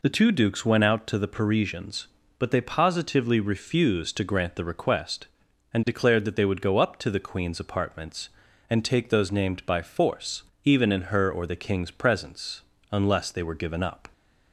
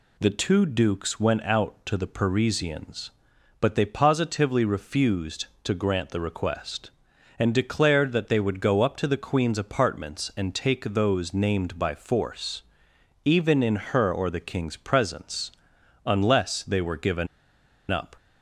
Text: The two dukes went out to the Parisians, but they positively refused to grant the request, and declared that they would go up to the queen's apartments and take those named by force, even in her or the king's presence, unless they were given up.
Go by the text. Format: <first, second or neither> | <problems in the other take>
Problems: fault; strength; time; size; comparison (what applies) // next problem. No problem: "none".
first | pauses between "given" and "up"; noticeable; at 17.2 s; 0.64 s long